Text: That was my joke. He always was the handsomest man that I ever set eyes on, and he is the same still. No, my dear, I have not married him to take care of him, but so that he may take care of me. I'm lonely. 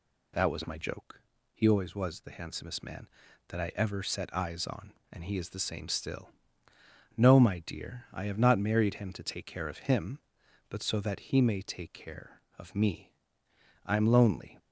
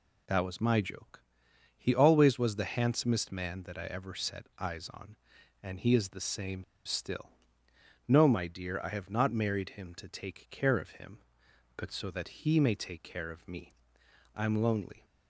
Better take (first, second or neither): first